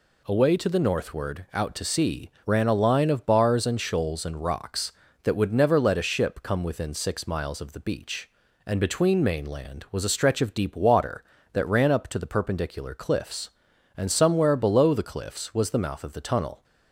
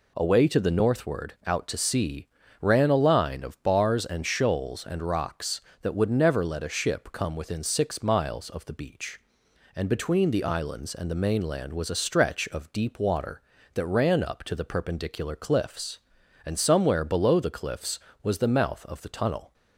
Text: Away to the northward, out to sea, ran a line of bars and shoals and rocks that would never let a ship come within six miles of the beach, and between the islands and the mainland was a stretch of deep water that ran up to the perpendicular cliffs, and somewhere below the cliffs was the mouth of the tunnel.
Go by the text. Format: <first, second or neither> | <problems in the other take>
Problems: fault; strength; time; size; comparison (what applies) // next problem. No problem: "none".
second | skips "the islands and the"; at 9.2 s